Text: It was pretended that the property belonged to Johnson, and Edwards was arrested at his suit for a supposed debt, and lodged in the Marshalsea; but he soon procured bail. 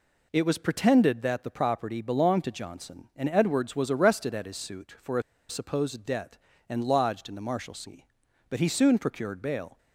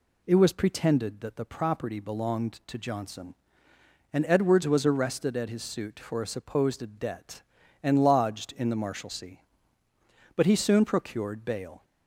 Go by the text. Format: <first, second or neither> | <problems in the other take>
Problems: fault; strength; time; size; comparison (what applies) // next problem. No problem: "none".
second | pauses between "a" and "supposed"; slight; at 5.2 s; 0.27 s long